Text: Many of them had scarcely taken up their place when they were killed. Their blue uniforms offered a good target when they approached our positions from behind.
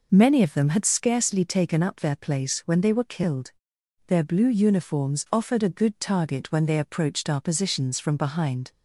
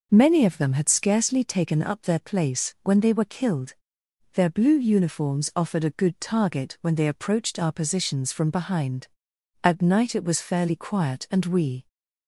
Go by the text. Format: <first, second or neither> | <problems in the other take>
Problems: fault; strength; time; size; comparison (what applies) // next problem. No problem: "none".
first | goes on to say "At night it was fairly quiet and we"; strong; from 9.6 s on; 2.2 s long